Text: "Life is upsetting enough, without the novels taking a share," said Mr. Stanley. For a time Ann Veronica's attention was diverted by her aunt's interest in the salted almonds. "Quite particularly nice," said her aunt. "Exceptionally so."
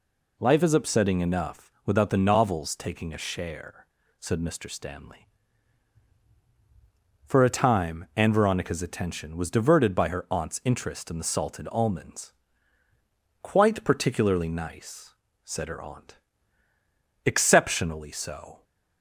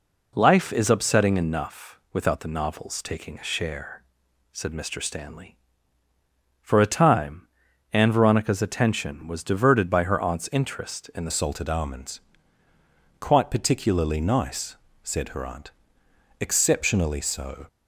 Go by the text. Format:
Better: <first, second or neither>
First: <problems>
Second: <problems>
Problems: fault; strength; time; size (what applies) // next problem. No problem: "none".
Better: first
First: none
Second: pauses between "time" and "Ann"; noticeable; at 7.4 s; 0.46 s long // changes voice at "salted"; from 11.2 s on; 6.4 s long